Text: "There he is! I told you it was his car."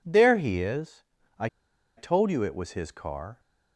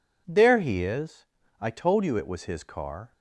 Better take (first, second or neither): second